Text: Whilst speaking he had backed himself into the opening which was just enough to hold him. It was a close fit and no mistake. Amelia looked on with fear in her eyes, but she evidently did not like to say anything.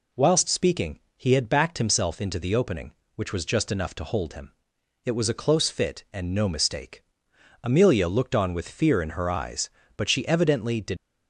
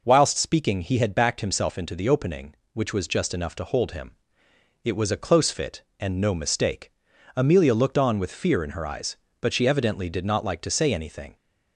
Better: second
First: pauses between "speaking" and "he"; slight; at 0.9 s; 0.16 s long // stops before "not like to say anything"; at 10.9 s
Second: none

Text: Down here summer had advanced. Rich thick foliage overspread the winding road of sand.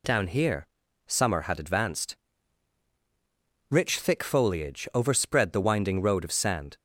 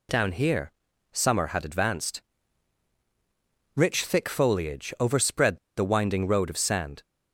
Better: first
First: pauses between "here" and "summer"; at 0.6 s; 0.39 s long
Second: pauses between "here" and "summer"; at 0.7 s; 0.40 s long // pauses between "overspread" and "the"; slight; at 5.5 s; 0.18 s long

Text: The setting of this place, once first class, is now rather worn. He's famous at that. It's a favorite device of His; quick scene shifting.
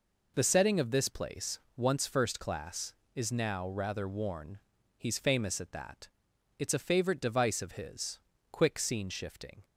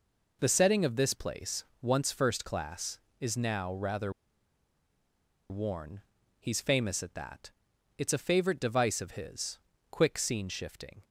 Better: first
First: none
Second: pauses between "rather" and "worn"; strong; at 4.1 s; 1.3 s long

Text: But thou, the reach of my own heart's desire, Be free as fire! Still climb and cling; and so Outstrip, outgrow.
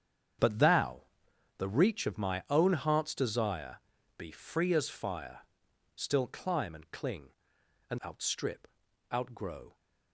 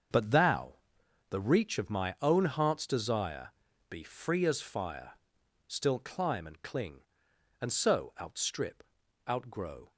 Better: second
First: starts louder than the rest; strong; until 1.9 s; 8 dB // skips "so"; at 8.0 s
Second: starts louder than the rest; until 1.6 s; 6.5 dB

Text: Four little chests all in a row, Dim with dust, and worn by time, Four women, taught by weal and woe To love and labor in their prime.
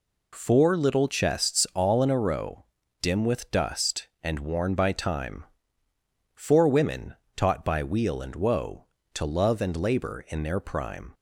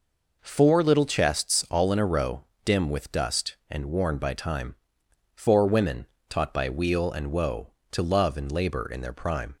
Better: neither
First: none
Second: none

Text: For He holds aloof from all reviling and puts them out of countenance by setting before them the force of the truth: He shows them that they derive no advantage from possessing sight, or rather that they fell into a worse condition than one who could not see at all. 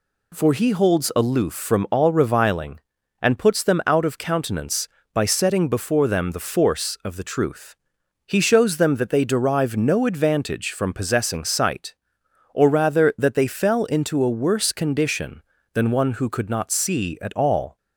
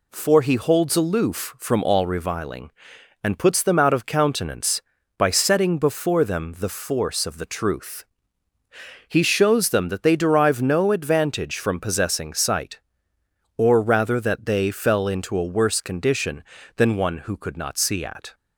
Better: first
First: none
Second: stops before "all"; at 18.3 s

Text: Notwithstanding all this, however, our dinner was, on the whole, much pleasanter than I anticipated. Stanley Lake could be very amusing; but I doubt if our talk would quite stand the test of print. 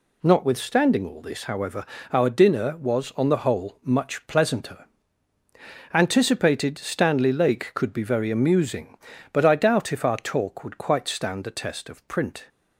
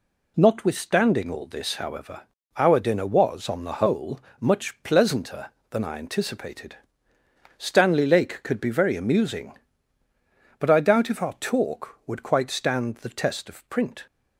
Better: second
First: skips "than I"; at 5.3 s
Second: none

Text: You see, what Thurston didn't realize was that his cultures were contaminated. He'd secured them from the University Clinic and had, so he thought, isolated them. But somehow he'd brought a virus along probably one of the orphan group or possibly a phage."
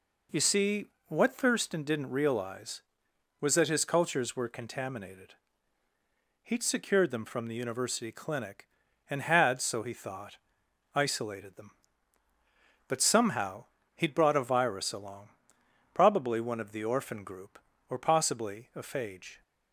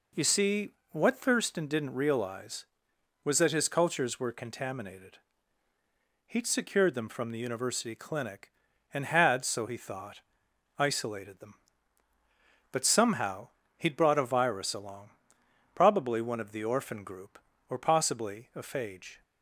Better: neither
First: pauses between "somehow" and "he'd"; slight; at 13.6 s; 0.29 s long // pauses between "along" and "probably"; noticeable; at 15.2 s; 0.64 s long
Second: pauses between "somehow" and "he'd"; slight; at 13.4 s; 0.28 s long // pauses between "along" and "probably"; noticeable; at 15.1 s; 0.64 s long

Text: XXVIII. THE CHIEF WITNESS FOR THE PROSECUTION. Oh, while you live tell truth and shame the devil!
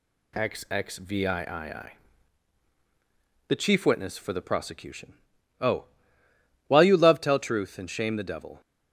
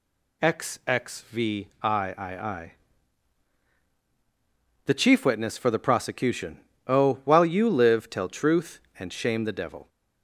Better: second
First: says "love" for "live"; at 6.9 s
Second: none

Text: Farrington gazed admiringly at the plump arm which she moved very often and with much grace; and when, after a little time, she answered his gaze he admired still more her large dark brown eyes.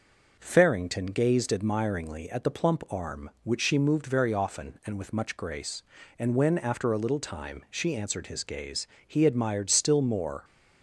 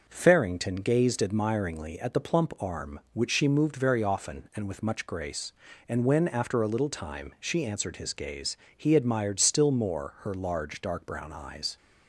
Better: second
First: pauses between "gaze" and "he"; slight; at 8.8 s; 0.18 s long // stops before "her large dark brown eyes"; at 10.4 s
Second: pauses between "gaze" and "he"; slight; at 8.5 s; 0.18 s long

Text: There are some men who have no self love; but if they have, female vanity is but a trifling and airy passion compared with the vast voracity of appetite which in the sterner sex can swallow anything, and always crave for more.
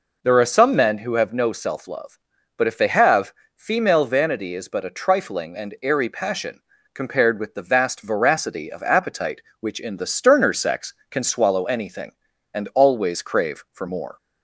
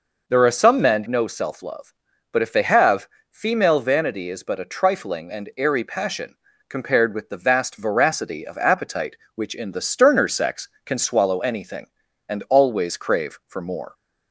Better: first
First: pauses between "passion" and "compared"; slight; at 6.6 s; 0.32 s long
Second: skips "who have"; at 1.0 s // pauses between "passion" and "compared"; slight; at 6.3 s; 0.32 s long

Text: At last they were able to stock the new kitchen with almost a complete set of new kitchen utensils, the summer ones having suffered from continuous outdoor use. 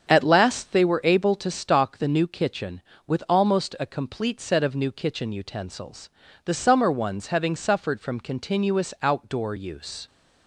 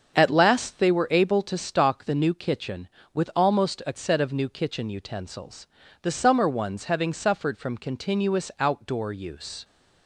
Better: first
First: starts louder than the rest; strong; until 1.1 s; 7.5 dB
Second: starts louder than the rest; until 1.1 s; 7 dB // skips "complete"; at 3.9 s

